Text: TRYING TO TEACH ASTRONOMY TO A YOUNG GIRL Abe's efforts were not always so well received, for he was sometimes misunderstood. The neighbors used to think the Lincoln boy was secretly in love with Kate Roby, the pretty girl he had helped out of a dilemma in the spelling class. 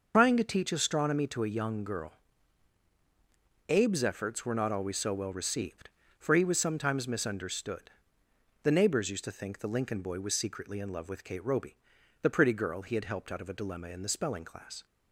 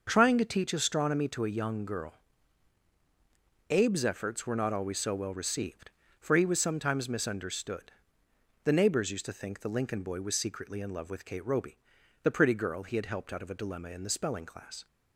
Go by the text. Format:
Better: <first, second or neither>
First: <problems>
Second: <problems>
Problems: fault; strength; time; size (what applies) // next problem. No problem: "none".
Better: second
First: loses the start of "TRYING"; at 0.1 s; 85 ms // starts louder than the rest; noticeable; until 1.1 s; 6 dB // pauses between "GIRL" and "Abe's"; strong; at 2.1 s; 1.5 s long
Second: starts louder than the rest; until 1.1 s; 6 dB // pauses between "GIRL" and "Abe's"; strong; at 2.1 s; 1.5 s long